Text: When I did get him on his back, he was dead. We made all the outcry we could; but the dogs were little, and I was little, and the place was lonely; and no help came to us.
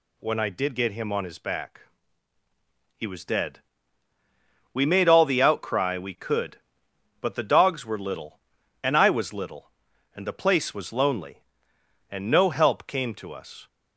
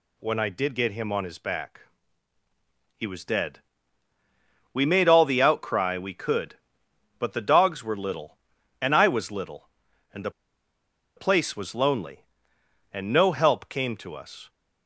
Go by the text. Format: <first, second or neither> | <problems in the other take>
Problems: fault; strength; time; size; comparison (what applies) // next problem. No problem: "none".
first | pauses between "the" and "place"; noticeable; at 10.3 s; 0.85 s long